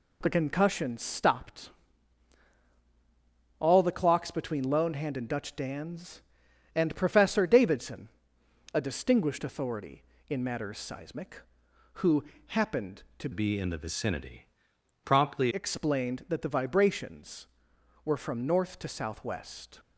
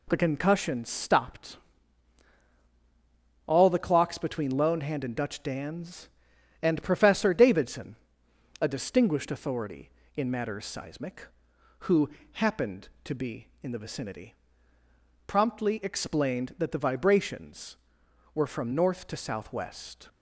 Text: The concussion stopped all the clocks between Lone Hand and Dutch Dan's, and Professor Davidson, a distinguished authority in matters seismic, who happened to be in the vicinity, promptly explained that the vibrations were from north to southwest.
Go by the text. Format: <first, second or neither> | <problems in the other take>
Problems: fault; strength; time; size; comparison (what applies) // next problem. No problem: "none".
second | pauses between "stopped" and "all"; strong; at 1.6 s; 1.8 s long; strong in the second // pauses between "who" and "happened"; slight; at 12.2 s; 0.24 s long; slight in the second // changes voice from "be" to "promptly"; from 13.3 to 15.5 s; 2.2 s long